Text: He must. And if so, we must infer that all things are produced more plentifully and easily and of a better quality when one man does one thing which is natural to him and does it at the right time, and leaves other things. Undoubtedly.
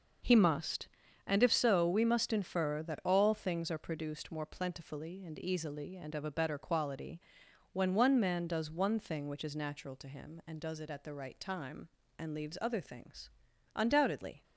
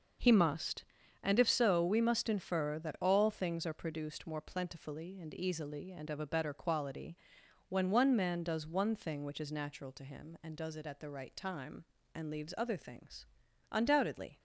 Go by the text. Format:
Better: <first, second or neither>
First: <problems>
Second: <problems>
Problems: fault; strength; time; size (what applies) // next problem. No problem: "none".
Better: neither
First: starts louder than the rest; noticeable; until 1.6 s; 6 dB // pauses between "quality" and "when"; noticeable; at 7.2 s; 0.52 s long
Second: starts louder than the rest; noticeable; until 1.5 s; 6 dB // pauses between "quality" and "when"; noticeable; at 7.1 s; 0.52 s long